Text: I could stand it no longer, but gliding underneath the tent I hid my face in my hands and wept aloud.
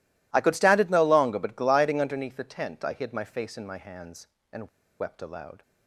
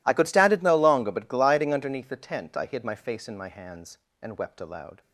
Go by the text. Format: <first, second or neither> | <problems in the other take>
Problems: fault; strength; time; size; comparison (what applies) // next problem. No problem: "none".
second | pauses between "and" and "wept"; slight; at 4.6 s; 0.31 s long